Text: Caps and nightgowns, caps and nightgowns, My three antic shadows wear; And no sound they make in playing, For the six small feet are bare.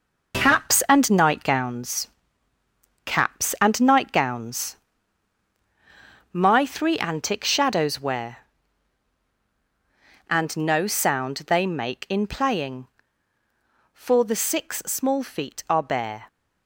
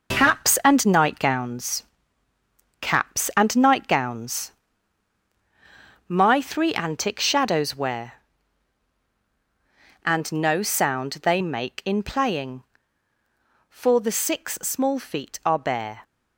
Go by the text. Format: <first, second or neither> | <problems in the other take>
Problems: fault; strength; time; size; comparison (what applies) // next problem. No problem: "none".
neither | none